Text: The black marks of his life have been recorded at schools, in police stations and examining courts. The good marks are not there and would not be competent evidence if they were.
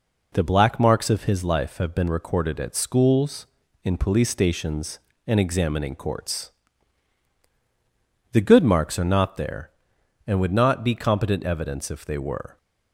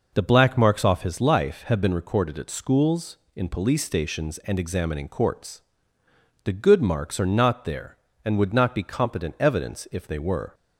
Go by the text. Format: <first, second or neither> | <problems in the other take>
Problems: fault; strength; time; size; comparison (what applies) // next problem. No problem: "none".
first | says "off" for "of"; at 0.8 s